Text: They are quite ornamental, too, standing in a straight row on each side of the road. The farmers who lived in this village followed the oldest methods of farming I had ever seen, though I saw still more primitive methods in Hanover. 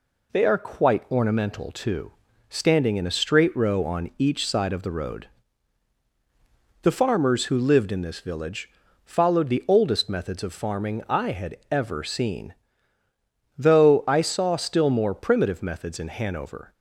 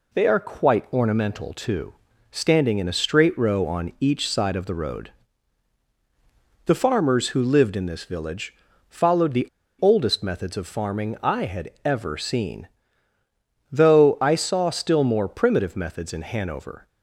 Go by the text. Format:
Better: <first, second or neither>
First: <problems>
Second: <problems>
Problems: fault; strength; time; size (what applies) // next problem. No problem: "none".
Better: first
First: pauses between "village" and "followed"; slight; at 8.6 s; 0.36 s long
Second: pauses between "village" and "followed"; slight; at 8.5 s; 0.36 s long // pauses between "the" and "oldest"; slight; at 9.4 s; 0.33 s long